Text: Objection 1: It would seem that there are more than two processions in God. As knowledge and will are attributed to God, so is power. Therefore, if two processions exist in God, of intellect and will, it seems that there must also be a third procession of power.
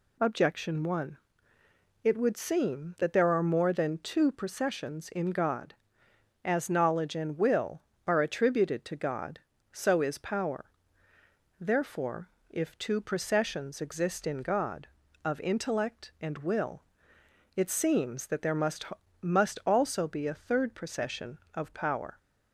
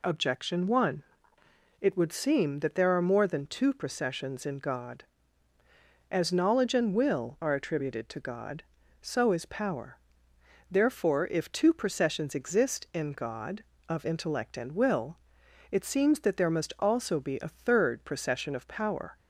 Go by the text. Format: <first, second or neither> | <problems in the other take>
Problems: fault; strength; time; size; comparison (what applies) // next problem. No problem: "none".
second | says "must" twice; at 19.2 s